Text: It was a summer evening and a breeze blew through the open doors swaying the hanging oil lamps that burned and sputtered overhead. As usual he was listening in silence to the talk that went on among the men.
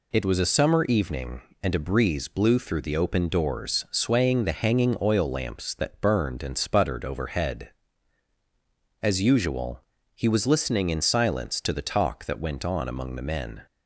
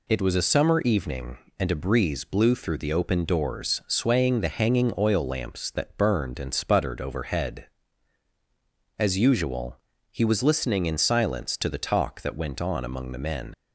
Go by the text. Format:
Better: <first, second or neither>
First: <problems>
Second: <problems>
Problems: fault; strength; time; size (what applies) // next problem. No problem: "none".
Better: first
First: pauses between "usual" and "he"; slight; at 9.8 s; 0.34 s long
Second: pauses between "usual" and "he"; slight; at 9.7 s; 0.34 s long // leaves "men" unfinished; at 13.5 s; 80 ms